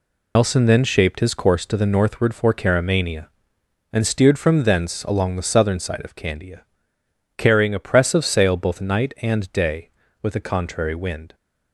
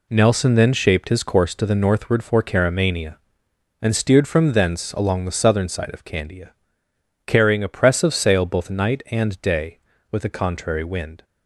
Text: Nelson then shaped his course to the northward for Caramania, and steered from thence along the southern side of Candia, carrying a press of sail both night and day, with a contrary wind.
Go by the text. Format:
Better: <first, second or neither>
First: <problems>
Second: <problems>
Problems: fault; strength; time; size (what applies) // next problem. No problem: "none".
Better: second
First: loses the start of "Nelson"; at 0.3 s; 145 ms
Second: none